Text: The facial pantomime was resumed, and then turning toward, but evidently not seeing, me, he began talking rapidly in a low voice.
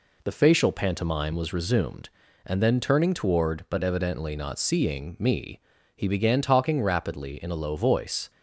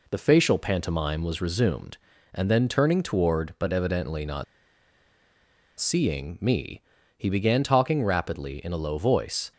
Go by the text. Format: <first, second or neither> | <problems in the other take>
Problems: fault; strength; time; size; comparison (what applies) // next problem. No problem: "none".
first | pauses between "not" and "seeing"; strong; at 4.4 s; 1.3 s long